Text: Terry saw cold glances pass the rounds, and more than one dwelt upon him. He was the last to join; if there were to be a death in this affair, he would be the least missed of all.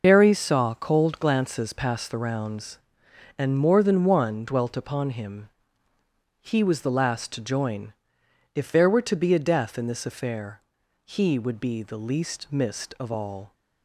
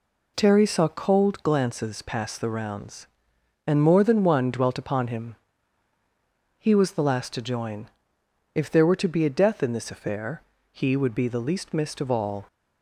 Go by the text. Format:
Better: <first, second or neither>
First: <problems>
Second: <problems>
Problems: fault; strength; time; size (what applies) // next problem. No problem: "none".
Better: second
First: loses the start of "Terry"; at 0.0 s; 70 ms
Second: none